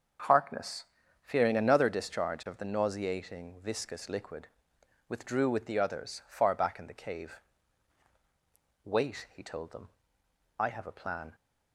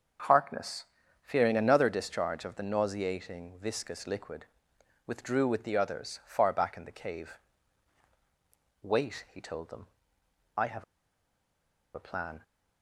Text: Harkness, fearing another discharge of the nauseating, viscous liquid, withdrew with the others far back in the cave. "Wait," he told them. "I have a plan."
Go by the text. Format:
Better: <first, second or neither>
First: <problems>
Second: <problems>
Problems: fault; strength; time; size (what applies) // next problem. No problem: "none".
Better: first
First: starts louder than the rest; until 1.6 s; 7 dB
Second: starts louder than the rest; until 1.6 s; 7 dB // pauses between "have" and "a"; at 10.8 s; 1.1 s long